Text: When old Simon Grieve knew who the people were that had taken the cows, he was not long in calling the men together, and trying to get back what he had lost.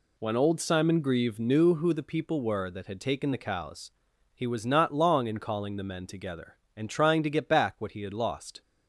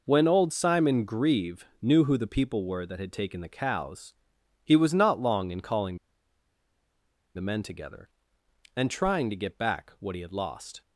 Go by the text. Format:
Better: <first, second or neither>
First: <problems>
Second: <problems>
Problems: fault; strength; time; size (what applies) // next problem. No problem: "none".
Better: first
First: none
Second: pauses between "Grieve" and "knew"; slight; at 1.6 s; 0.16 s long // pauses between "calling" and "the"; strong; at 5.9 s; 1.3 s long